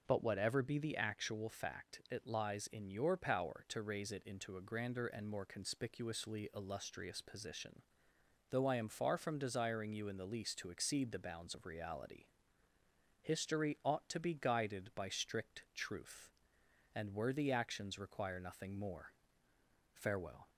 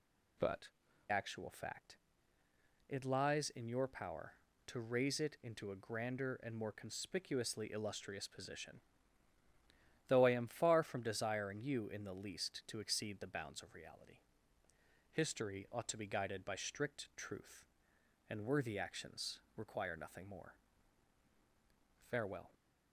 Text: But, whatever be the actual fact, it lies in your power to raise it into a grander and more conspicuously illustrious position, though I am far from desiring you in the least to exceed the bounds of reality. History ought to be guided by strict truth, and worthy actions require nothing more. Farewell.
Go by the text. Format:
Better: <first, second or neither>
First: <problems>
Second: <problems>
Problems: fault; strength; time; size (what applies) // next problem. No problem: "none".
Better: first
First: none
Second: skips "whatever be the"; at 0.8 s // pauses between "actions" and "require"; slight; at 19.3 s; 0.16 s long